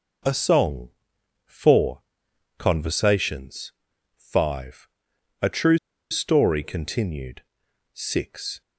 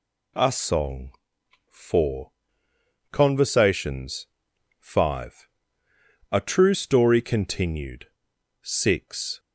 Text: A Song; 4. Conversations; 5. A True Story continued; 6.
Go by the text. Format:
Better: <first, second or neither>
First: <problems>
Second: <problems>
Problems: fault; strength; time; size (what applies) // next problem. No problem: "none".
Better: second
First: pauses between "True" and "Story"; slight; at 5.7 s; 0.34 s long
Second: none